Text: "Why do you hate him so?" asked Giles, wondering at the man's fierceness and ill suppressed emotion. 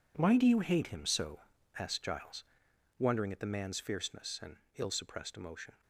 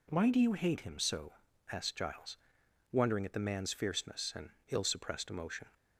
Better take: second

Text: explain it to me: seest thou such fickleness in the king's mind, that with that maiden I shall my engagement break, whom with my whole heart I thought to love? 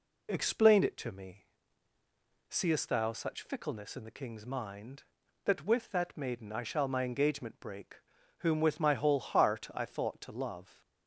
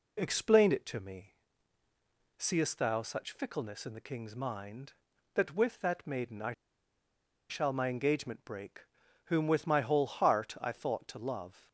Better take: first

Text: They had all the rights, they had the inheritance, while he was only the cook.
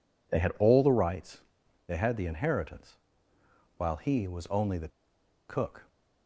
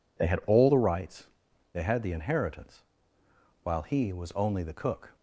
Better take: second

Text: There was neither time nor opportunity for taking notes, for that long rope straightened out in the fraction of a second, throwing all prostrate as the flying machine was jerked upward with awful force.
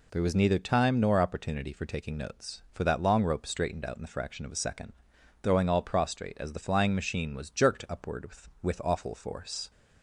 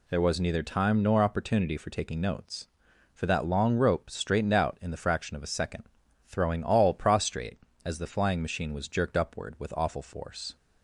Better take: second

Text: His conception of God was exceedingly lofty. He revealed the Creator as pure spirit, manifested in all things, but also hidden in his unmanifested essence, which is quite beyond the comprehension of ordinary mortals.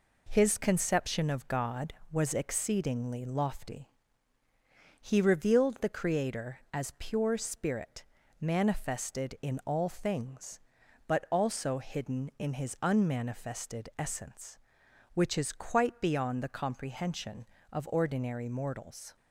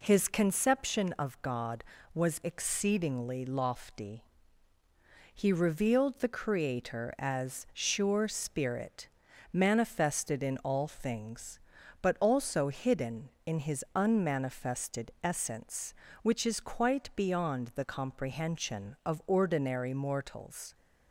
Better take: first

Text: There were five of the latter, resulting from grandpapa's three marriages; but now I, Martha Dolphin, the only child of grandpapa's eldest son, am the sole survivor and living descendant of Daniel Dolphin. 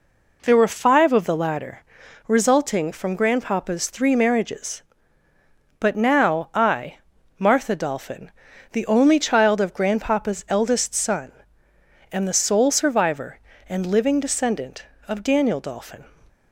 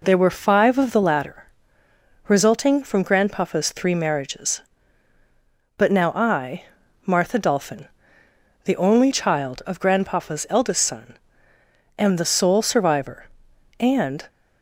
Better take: first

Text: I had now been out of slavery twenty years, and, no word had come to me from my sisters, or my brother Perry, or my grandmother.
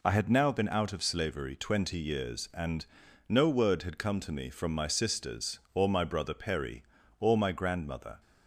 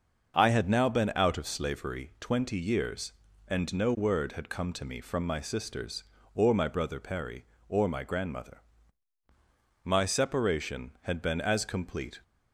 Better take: first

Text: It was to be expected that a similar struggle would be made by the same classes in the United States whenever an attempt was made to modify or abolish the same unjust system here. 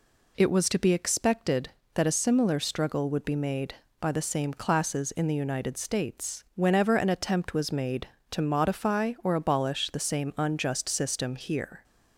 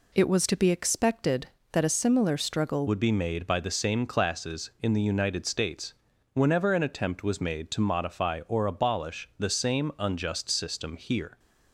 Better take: first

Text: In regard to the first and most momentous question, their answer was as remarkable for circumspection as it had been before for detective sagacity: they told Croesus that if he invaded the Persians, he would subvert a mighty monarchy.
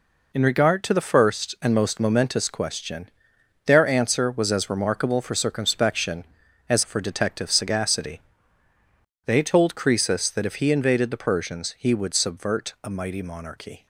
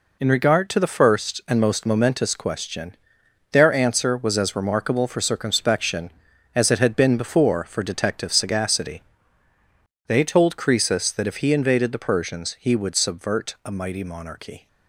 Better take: second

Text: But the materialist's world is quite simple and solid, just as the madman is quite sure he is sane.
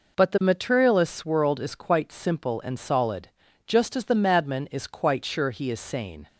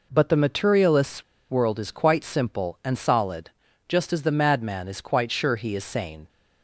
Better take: first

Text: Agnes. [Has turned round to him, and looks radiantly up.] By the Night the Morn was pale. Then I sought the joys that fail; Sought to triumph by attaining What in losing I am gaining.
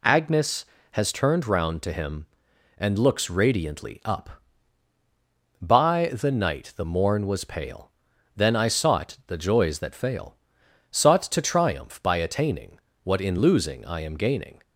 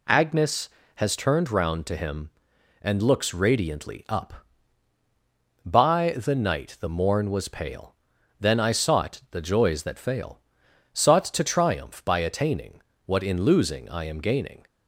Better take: neither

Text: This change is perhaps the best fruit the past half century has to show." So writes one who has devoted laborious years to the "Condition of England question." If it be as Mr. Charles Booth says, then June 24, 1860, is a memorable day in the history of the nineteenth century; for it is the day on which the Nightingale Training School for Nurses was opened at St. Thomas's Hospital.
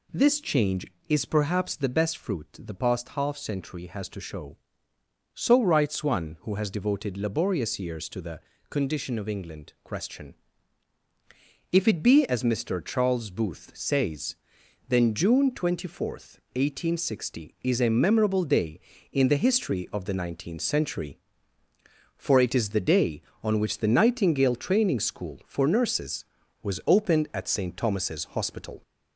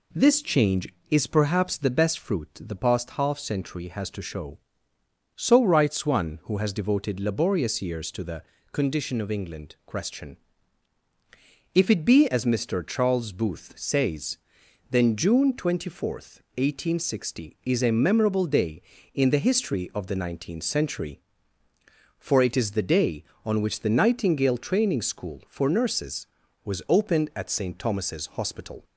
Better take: second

